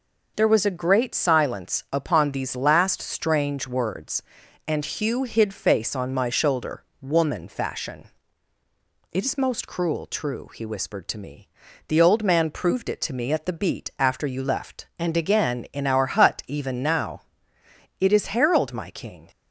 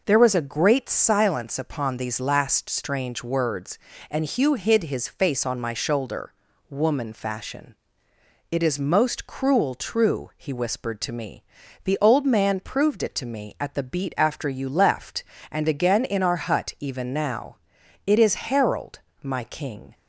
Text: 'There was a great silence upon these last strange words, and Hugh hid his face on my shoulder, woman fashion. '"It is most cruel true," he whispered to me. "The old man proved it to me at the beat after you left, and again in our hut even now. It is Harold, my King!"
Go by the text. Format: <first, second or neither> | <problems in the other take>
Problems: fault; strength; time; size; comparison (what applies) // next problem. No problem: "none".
second | skips "his"; at 5.5 s